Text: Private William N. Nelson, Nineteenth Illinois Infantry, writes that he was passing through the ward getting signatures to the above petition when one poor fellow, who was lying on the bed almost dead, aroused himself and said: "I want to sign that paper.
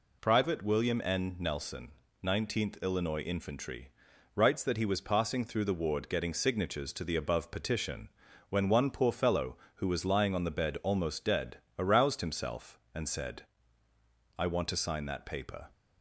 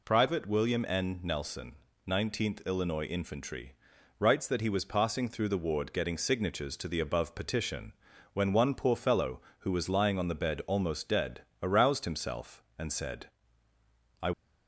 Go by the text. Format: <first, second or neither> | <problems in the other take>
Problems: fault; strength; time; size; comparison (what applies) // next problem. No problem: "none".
first | pauses between "petition" and "when"; at 7.9 s; 0.40 s long; also in the first // stops before "want to sign that paper"; at 14.3 s